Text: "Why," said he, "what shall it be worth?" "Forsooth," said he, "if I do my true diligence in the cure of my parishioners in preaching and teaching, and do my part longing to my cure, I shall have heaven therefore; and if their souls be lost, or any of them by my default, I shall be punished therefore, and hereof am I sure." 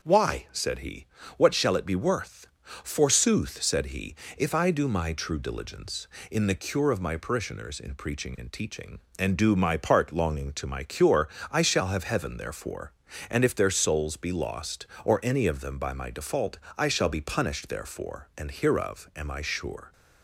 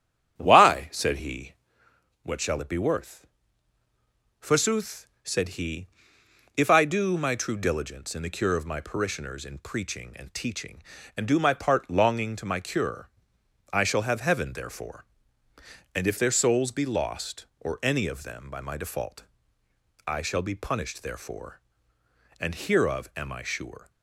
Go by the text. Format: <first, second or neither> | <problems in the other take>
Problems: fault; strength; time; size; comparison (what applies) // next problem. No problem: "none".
first | starts louder than the rest; strong; until 1.8 s; 9.5 dB